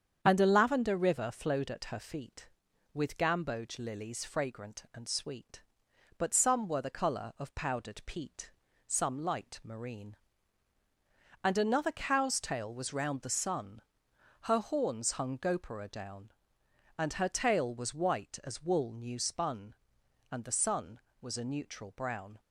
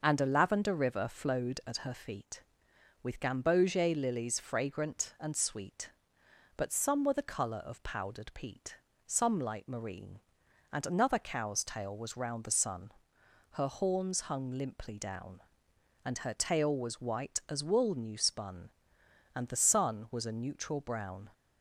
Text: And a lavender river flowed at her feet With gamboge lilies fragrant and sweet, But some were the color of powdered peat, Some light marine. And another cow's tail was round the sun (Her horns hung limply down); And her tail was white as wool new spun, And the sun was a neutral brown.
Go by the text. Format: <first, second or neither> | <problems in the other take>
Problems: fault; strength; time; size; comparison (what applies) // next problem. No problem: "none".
second | starts louder than the rest; strong; until 1.2 s; 8 dB // says "gopura" for "limply"; at 15.3 s